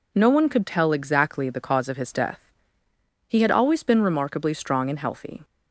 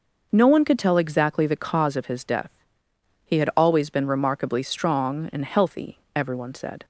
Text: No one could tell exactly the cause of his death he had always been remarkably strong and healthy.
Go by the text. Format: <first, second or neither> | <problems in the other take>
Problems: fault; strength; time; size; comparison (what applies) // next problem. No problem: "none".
first | pauses between "death" and "he"; noticeable; at 2.5 s; 0.74 s long; noticeable in the first // goes on to say "Everyone said"; noticeable; from 6.1 s on; 0.70 s long